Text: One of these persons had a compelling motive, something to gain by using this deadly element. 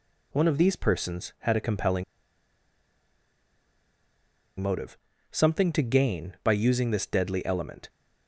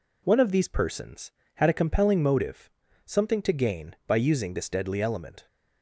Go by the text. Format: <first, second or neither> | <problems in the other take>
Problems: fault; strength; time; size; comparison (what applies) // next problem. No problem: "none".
second | pauses between "compelling" and "motive"; strong; at 2.0 s; 2.5 s long